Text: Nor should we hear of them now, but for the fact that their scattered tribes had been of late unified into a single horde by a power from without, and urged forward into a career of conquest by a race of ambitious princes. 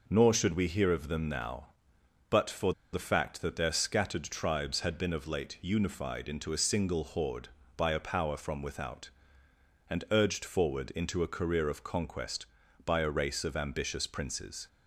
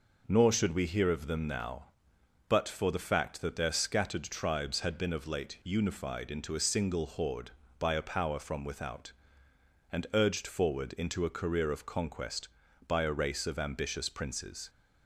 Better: second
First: pauses between "for" and "the"; slight; at 2.7 s; 0.20 s long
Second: none

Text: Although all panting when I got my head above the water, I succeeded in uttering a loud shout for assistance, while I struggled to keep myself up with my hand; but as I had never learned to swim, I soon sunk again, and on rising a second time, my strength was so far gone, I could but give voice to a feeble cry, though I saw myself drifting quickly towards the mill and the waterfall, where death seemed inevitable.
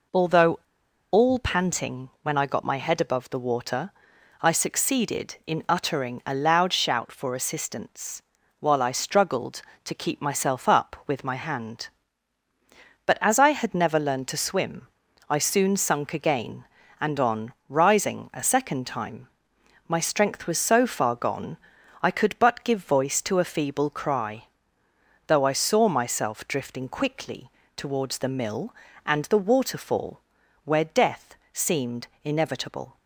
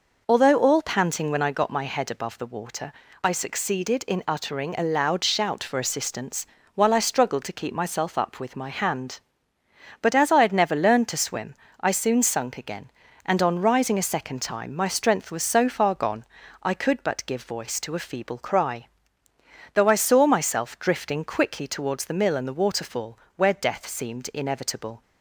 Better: second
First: pauses between "Although" and "all"; noticeable; at 0.5 s; 0.55 s long // pauses between "on" and "rising"; slight; at 17.5 s; 0.16 s long // pauses between "quickly" and "towards"; slight; at 27.4 s; 0.26 s long // pauses between "death" and "seemed"; slight; at 31.3 s; 0.18 s long // pauses between "seemed" and "inevitable"; slight; at 32.0 s; 0.16 s long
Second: none

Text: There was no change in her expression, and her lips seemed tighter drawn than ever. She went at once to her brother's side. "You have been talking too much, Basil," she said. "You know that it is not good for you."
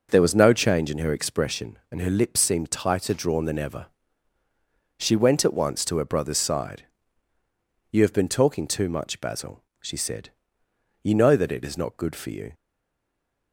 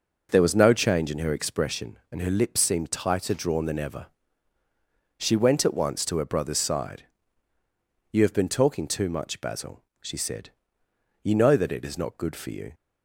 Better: second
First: stays silent after the last word; slight; from 12.5 s on; 1.0 s long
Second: none

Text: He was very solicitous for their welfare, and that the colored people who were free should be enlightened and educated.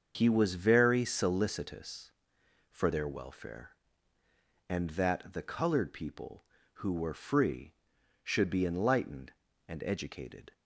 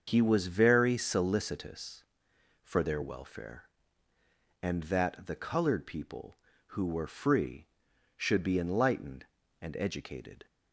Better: neither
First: starts louder than the rest; until 1.1 s; 6.5 dB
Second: starts louder than the rest; until 1.0 s; 6.5 dB

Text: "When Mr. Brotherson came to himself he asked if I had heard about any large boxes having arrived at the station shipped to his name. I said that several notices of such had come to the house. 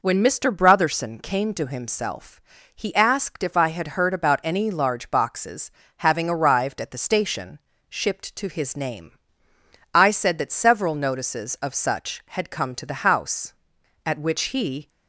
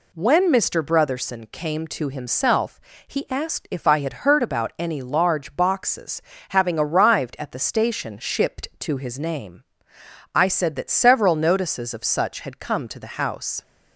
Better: second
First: pauses between "himself" and "he"; slight; at 2.4 s; 0.32 s long // pauses between "boxes" and "having"; slight; at 5.7 s; 0.28 s long // pauses between "station" and "shipped"; slight; at 7.6 s; 0.28 s long // goes on to say "At which he"; noticeable; from 14.0 s on; 0.84 s long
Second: pauses between "himself" and "he"; slight; at 2.7 s; 0.30 s long // pauses between "boxes" and "having"; slight; at 6.2 s; 0.30 s long

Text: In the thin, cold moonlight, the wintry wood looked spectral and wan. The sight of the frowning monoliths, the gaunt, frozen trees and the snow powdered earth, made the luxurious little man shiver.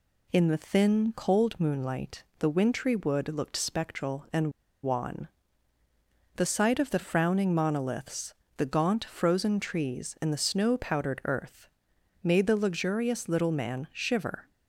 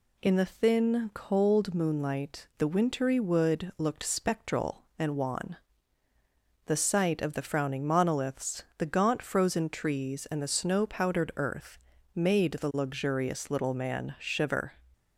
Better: second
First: pauses between "and" and "wan"; slight; at 4.5 s; 0.32 s long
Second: none

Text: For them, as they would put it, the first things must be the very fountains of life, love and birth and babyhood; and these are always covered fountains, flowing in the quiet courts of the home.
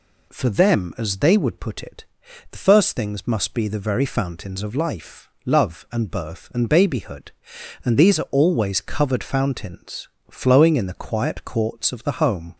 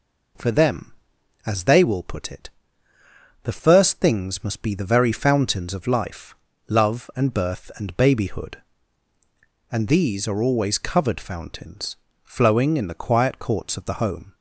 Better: first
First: none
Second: says "will" for "would"; at 1.8 s

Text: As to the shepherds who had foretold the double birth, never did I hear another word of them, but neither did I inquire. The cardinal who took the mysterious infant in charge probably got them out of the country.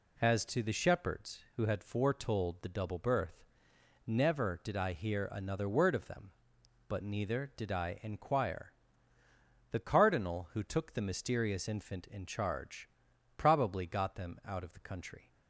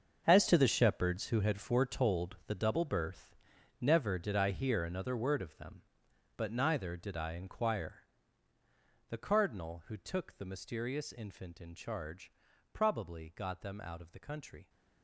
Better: first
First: pauses between "charge" and "probably"; noticeable; at 12.8 s; 0.48 s long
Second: gets quieter; strong; throughout; 13.5 dB // pauses between "charge" and "probably"; at 12.3 s; 0.40 s long

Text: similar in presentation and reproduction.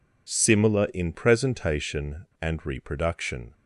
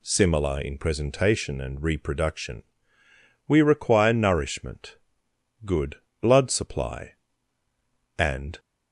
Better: first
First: none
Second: goes on to say "We require nourishment good blood supply and"; strong; from 3.4 s on; 5.1 s long

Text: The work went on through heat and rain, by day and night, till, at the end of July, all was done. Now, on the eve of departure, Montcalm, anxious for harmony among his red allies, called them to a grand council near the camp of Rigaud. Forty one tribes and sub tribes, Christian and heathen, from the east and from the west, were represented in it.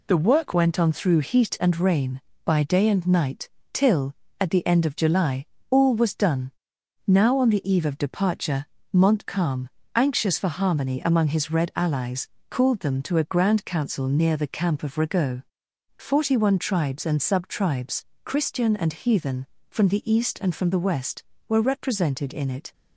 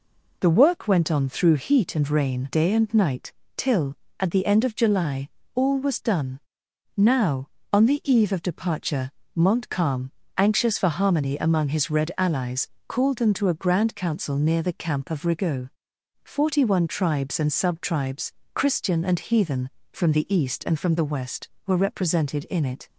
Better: first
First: none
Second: skips "by"; at 2.4 s

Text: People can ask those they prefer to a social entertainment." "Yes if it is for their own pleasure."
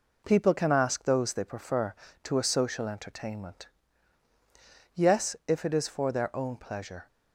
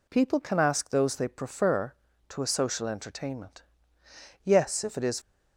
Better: first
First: none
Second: stops before "for their own pleasure"; at 5.2 s

